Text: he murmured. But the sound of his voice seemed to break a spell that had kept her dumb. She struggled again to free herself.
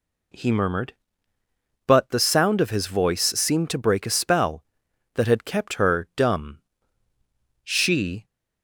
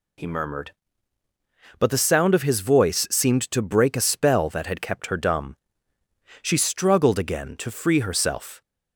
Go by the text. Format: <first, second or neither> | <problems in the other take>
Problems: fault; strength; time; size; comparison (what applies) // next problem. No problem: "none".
second | stops before "struggled again to free herself"; at 8.2 s